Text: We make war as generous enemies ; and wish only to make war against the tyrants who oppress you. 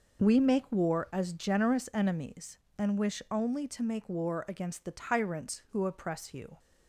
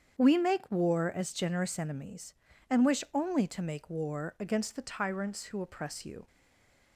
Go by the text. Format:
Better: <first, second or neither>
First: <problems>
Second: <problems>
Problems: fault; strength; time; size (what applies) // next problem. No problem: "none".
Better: first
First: none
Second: starts louder than the rest; strong; until 1.2 s; 8 dB // stays silent after the last word; slight; from 6.2 s on; 0.7 s long